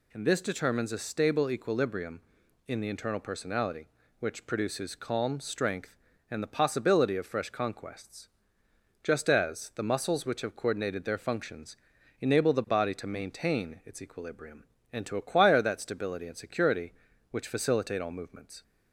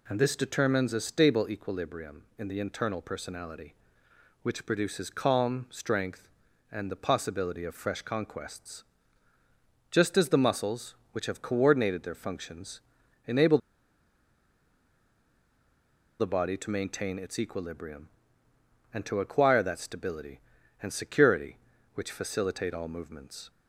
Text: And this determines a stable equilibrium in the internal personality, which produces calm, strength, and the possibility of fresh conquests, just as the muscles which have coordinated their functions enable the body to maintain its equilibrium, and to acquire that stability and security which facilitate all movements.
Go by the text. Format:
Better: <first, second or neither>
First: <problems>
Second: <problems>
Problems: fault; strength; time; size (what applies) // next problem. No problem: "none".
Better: first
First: pauses between "functions" and "enable"; at 11.7 s; 0.44 s long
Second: pauses between "functions" and "enable"; noticeable; at 12.8 s; 0.46 s long // pauses between "enable" and "the"; strong; at 13.5 s; 2.6 s long